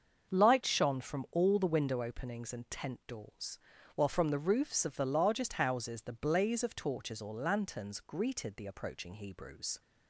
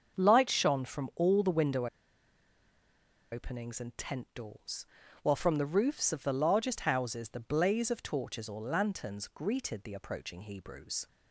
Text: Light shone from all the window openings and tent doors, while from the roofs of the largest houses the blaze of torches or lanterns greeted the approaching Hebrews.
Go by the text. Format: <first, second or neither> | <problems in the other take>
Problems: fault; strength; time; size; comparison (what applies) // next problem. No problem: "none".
first | starts louder than the rest; until 1.2 s; 6.5 dB; also in the first // pauses between "window" and "openings"; strong; at 1.8 s; 1.4 s long